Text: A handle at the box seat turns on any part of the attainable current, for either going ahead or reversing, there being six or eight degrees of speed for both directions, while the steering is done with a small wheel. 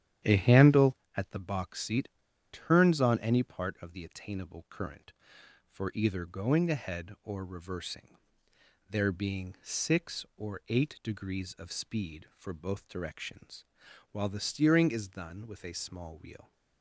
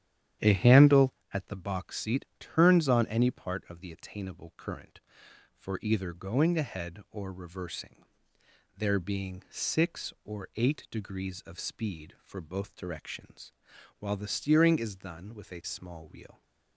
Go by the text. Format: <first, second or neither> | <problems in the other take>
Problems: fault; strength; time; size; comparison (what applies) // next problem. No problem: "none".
second | starts louder than the rest; strong; until 1.4 s; 10.5 dB; strong in the second // pauses between "seat" and "turns"; at 2.0 s; 0.44 s long